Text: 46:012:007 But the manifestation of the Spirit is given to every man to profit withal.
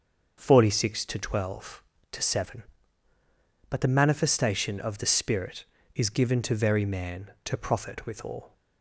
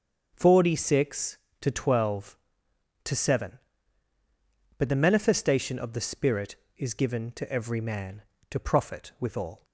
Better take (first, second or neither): second